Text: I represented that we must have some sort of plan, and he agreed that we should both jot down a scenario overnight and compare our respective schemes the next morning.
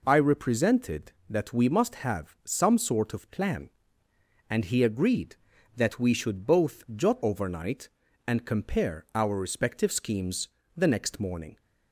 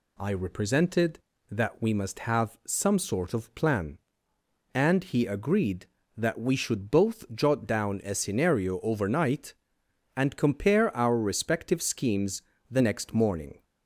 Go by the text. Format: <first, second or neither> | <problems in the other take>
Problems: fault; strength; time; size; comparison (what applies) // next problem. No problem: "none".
second | skips "down a scenario"; at 7.2 s // pauses between "schemes" and "the"; slight; at 10.4 s; 0.28 s long; slight in the second